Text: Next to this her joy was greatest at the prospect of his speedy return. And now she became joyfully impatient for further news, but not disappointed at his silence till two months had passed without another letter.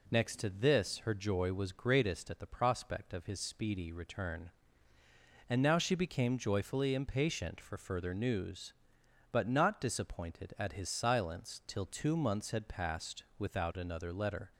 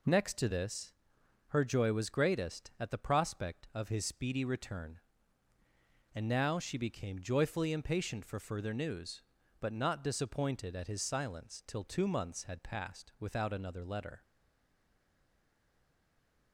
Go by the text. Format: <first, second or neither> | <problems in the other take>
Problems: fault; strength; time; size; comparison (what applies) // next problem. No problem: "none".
first | pauses between "this" and "her"; noticeable; at 0.9 s; 0.56 s long // stays silent after the last word; from 14.2 s on; 2.3 s long